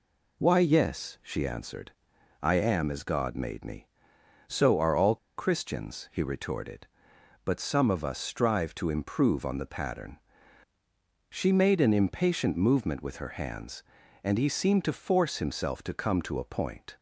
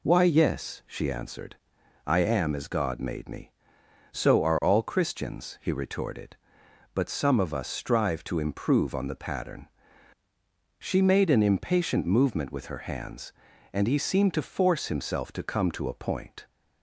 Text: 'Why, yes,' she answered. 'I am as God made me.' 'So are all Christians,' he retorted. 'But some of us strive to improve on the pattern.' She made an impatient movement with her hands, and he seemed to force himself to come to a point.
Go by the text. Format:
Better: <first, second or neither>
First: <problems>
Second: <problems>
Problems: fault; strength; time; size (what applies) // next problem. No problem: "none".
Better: second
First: pauses between "all" and "Christians"; slight; at 5.1 s; 0.20 s long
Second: none